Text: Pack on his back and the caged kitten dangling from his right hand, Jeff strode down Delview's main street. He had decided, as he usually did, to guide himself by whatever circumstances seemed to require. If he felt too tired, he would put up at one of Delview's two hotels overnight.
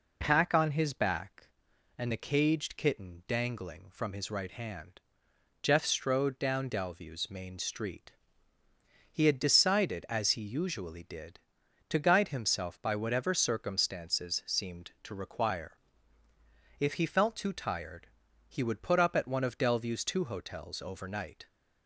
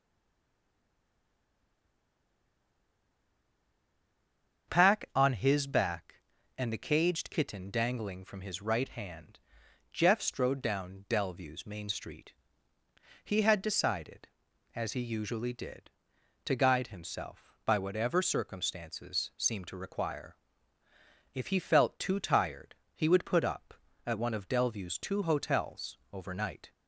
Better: first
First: none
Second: stays silent before the first word; strong; until 4.6 s; 4.6 s long // starts louder than the rest; until 5.7 s; 6.5 dB

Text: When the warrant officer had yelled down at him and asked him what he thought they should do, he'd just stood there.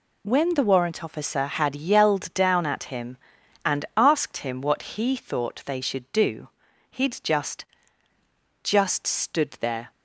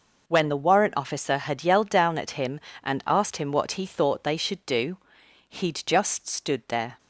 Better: second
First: says "just" twice; at 8.6 s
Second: none

